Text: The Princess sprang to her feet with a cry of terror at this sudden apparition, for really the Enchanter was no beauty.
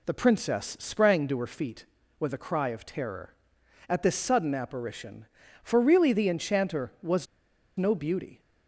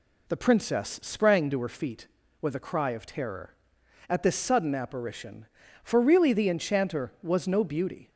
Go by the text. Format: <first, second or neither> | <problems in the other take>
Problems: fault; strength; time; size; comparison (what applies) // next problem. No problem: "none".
second | pauses between "was" and "no"; noticeable; at 7.2 s; 0.51 s long